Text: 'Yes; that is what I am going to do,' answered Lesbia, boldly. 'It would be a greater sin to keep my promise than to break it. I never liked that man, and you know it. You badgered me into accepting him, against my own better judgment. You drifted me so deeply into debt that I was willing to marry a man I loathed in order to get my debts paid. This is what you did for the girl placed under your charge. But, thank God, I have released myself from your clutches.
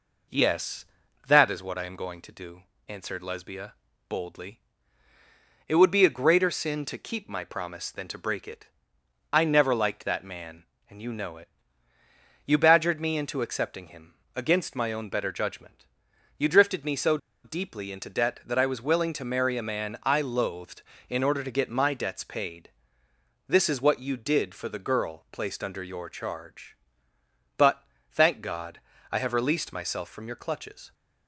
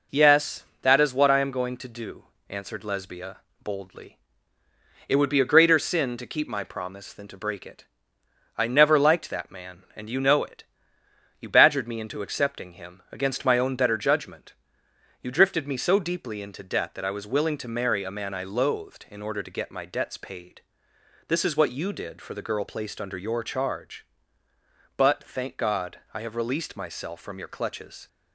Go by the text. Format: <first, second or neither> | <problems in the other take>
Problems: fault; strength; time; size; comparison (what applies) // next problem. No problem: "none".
second | pauses between "so" and "deeply"; slight; at 17.1 s; 0.26 s long